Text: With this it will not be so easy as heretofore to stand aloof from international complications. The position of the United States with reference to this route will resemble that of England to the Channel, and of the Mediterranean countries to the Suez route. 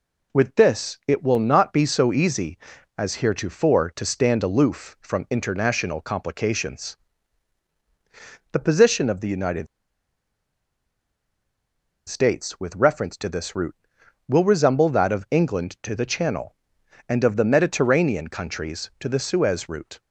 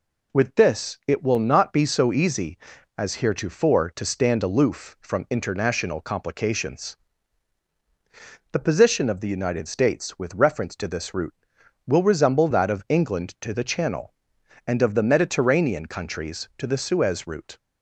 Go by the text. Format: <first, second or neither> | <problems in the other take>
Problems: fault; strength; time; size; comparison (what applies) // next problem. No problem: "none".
second | pauses between "United" and "States"; strong; at 9.6 s; 2.4 s long